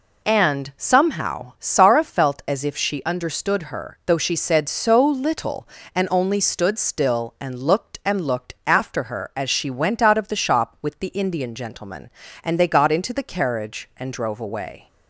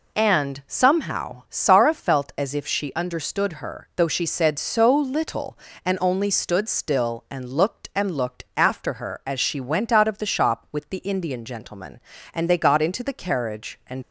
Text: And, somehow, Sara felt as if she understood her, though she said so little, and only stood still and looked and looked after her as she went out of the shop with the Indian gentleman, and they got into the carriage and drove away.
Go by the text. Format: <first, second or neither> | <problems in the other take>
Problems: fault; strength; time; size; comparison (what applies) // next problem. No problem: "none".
first | stops before "drove away"; at 14.0 s